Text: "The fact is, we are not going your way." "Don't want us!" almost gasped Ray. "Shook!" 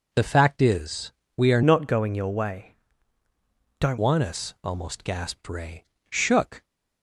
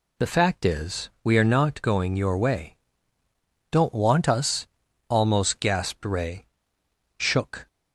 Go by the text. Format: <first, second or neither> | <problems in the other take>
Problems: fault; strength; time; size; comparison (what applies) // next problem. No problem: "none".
second | changes voice from "not" to "Don't"; from 1.6 to 3.9 s; 2.3 s long